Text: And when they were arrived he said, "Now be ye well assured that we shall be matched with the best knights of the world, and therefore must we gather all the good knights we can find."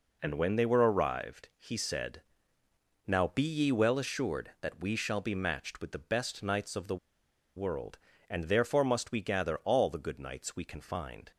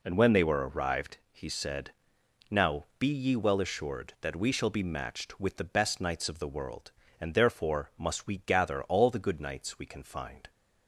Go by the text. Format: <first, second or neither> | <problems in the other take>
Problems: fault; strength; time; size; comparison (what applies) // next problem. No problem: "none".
second | pauses between "the" and "world"; noticeable; at 6.9 s; 0.59 s long